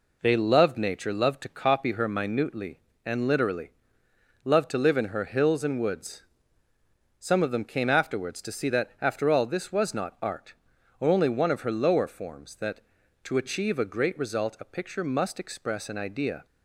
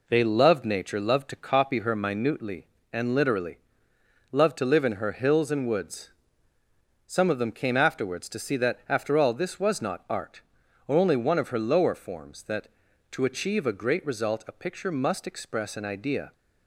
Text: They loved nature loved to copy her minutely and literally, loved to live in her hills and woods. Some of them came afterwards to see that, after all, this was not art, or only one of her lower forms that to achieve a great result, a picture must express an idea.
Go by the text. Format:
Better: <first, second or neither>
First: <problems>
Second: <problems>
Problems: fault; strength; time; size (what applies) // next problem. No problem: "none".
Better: neither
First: none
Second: none